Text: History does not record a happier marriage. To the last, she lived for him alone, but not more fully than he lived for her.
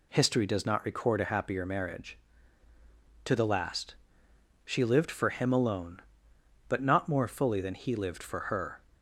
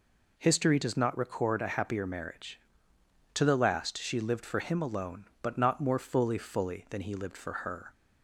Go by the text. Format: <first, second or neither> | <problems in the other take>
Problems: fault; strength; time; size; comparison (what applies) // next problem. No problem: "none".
first | says "fully" twice; at 6.3 s